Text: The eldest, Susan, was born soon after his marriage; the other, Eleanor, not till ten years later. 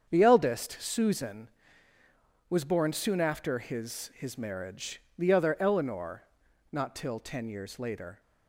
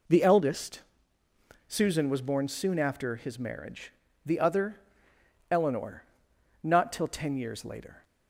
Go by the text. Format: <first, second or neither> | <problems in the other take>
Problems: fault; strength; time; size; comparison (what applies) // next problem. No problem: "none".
second | starts louder than the rest; strong; until 1.1 s; 7.5 dB // says "his" twice; at 4.1 s